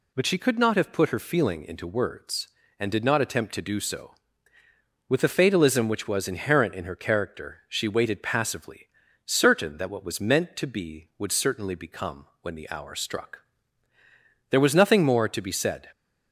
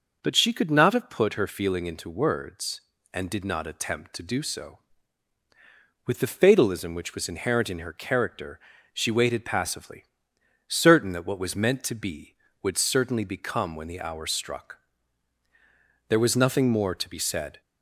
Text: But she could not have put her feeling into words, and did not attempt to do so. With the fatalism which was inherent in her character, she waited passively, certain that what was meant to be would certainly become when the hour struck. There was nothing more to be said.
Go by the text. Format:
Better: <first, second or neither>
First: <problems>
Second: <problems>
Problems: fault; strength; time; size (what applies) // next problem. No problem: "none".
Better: neither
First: none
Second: none